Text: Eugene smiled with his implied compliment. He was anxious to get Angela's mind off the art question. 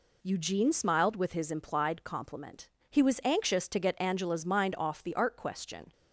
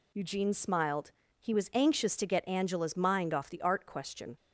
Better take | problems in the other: first | skips "with his implied compliment"; at 1.2 s

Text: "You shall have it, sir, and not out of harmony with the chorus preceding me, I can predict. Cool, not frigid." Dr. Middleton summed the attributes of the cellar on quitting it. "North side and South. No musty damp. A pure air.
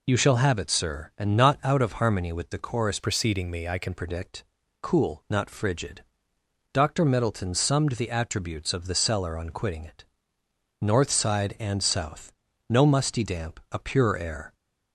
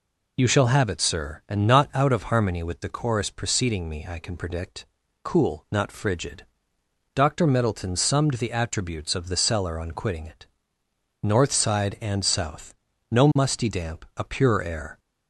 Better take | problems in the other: second | changes voice from "preceding" to "can"; from 2.9 to 3.9 s; 1.0 s long

